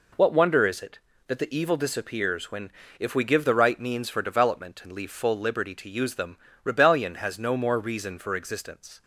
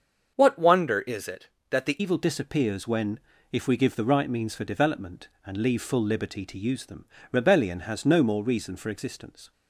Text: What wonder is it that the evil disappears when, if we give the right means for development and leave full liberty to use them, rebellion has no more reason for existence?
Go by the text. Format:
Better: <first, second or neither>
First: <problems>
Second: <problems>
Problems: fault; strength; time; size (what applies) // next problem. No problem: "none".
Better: first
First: none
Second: starts louder than the rest; until 1.3 s; 7 dB // changes voice at "evil"; from 1.9 s on; 7.6 s long